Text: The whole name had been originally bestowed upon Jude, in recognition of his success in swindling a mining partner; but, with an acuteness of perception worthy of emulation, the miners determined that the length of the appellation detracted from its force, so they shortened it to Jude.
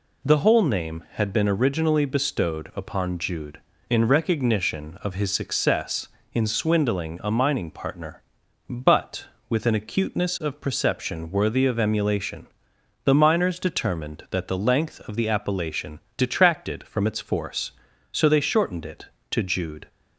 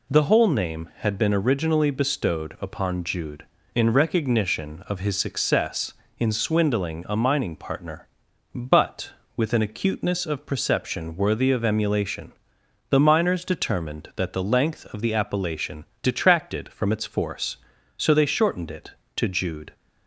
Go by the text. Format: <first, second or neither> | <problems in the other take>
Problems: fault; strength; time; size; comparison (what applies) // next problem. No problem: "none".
neither | pauses between "appellation" and "detracted"; slight; the same in both